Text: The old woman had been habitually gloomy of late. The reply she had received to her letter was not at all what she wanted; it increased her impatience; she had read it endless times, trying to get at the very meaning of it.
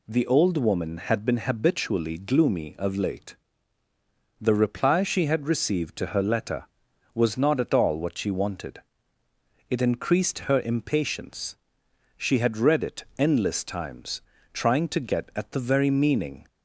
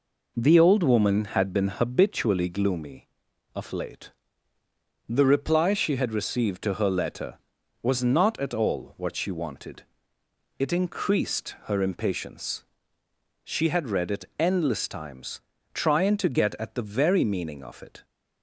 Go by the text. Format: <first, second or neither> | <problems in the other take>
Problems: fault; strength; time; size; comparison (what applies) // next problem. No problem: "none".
second | stops before "of it"; at 16.4 s